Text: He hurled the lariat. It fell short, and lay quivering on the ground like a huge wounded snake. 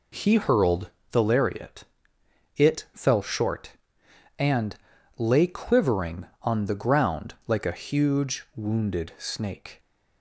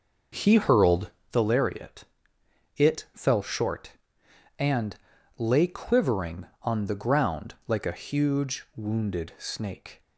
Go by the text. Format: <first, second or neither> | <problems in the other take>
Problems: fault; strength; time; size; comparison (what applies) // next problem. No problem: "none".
first | starts louder than the rest; noticeable; until 1.3 s; 5.5 dB // pauses between "hurled" and "the"; slight; at 1.1 s; 0.18 s long; slight in the first // pauses between "and" and "lay"; at 4.9 s; 0.42 s long; also in the first